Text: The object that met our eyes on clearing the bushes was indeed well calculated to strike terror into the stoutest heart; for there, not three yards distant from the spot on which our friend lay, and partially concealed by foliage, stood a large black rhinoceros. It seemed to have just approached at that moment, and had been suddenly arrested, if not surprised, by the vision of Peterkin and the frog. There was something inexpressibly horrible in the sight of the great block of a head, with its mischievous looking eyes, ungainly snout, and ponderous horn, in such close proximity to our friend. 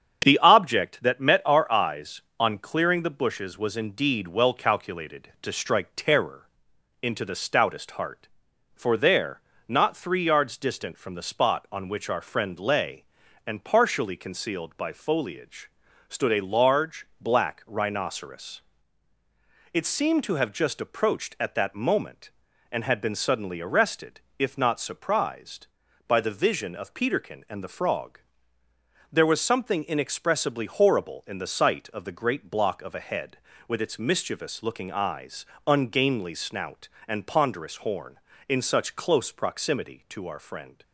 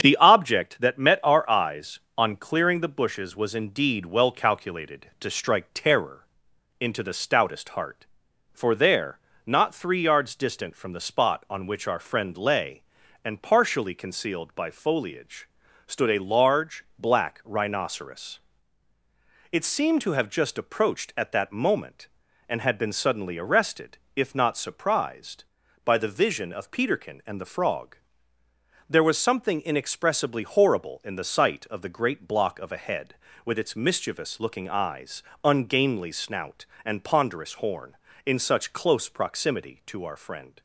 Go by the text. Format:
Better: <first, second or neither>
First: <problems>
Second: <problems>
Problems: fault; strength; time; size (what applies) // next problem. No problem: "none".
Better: neither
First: starts louder than the rest; strong; until 1.2 s; 8 dB // pauses between "terror" and "into"; noticeable; at 6.4 s; 0.54 s long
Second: starts louder than the rest; strong; until 1.0 s; 8 dB // pauses between "terror" and "into"; noticeable; at 6.2 s; 0.54 s long